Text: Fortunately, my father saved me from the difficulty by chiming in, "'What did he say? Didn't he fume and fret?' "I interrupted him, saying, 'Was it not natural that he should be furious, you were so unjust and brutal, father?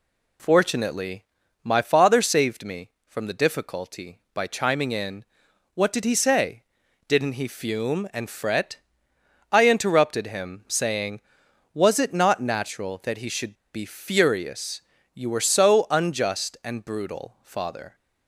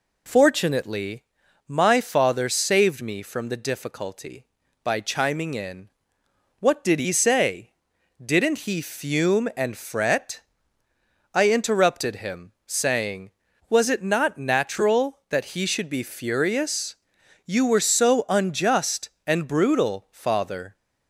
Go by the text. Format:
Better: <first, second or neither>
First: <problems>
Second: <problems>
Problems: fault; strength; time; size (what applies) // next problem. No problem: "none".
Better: second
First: pauses between "should" and "be"; slight; at 13.5 s; 0.21 s long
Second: none